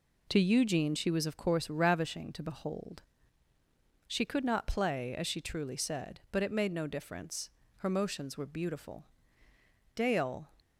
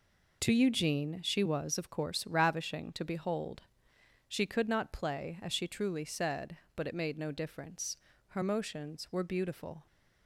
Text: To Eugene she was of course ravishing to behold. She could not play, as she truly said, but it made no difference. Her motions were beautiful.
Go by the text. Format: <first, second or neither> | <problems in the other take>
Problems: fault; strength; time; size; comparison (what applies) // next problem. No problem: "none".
second | goes on to say "Dale"; from 9.9 s on; 0.54 s long